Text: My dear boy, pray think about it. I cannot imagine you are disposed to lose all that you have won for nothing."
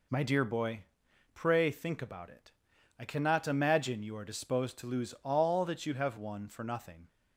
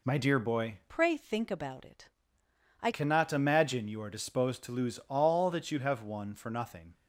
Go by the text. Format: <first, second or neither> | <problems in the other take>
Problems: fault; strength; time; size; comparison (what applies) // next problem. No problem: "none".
first | changes voice from "pray" to "I"; from 0.8 to 2.9 s; 2.1 s long